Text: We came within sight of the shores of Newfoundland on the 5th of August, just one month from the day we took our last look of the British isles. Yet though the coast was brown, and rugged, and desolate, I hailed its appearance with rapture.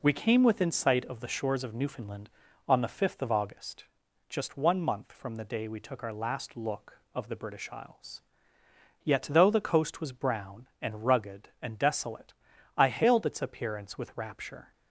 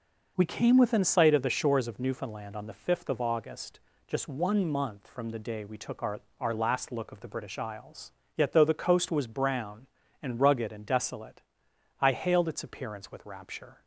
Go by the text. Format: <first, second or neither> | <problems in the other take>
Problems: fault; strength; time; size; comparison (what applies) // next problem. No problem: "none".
first | says "our" twice; at 6.4 s